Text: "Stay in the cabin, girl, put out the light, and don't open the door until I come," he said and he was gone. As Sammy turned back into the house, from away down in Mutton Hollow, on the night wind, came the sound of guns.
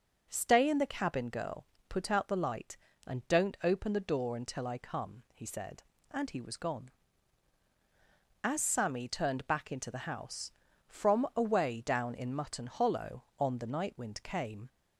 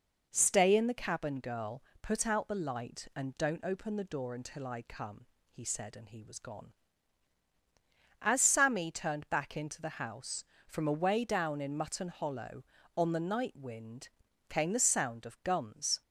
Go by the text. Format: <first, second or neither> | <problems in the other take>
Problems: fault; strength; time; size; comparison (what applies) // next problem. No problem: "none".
second | stops before "the sound of guns"; at 14.6 s